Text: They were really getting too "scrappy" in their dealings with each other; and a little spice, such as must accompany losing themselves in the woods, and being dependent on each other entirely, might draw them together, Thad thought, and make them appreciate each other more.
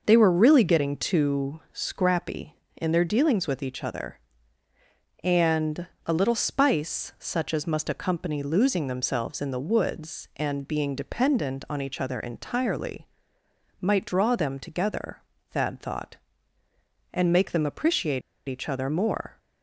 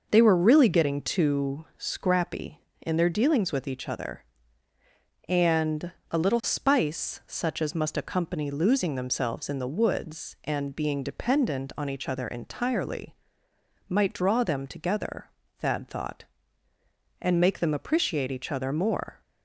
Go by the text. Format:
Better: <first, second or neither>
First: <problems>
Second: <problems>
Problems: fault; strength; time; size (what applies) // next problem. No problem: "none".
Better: second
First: pauses between "and" and "a"; slight; at 5.8 s; 0.22 s long // pauses between "appreciate" and "each"; slight; at 18.2 s; 0.27 s long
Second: pauses between "and" and "a"; slight; at 5.8 s; 0.22 s long